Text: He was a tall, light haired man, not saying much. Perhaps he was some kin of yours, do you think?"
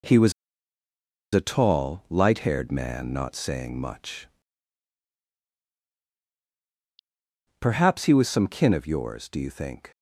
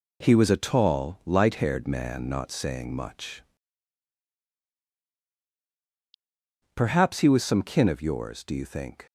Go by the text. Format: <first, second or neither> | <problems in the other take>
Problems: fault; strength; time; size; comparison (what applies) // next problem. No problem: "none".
second | pauses between "was" and "a"; at 0.3 s; 1.0 s long